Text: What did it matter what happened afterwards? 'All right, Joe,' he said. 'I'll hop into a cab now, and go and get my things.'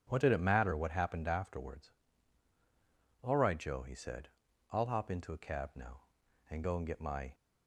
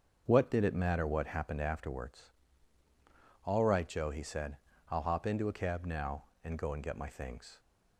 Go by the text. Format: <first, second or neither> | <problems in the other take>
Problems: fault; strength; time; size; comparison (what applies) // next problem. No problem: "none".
second | starts louder than the rest; strong; until 1.0 s; 9 dB; also in the second // stops before "things"; at 7.3 s